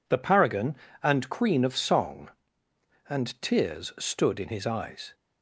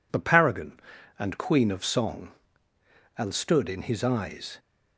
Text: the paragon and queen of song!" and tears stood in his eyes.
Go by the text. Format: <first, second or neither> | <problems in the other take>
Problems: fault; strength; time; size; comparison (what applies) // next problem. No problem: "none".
first | skips "tears"; at 3.3 s